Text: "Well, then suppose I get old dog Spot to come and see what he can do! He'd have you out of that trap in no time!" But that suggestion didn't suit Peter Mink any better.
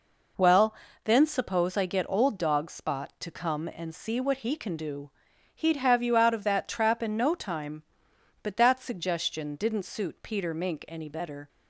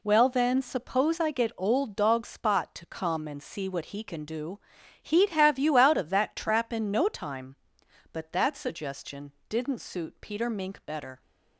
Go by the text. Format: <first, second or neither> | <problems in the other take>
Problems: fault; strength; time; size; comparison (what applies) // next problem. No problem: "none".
first | pauses between "suggestion" and "didn't"; slight; at 9.3 s; 0.20 s long // skips "any"; at 10.8 s